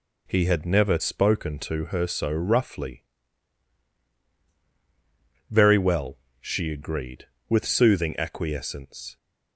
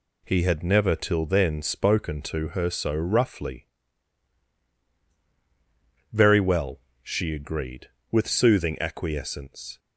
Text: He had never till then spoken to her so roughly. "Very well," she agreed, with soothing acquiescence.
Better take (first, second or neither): second